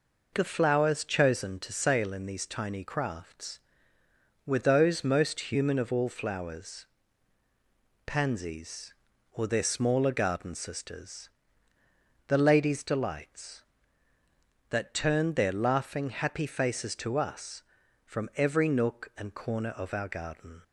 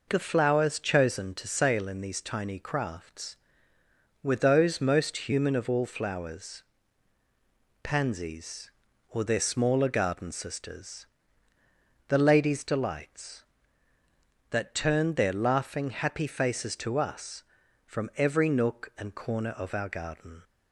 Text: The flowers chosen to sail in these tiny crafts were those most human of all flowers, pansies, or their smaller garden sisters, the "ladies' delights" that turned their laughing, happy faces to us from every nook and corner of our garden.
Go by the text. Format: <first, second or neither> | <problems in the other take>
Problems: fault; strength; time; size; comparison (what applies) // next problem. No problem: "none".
neither | none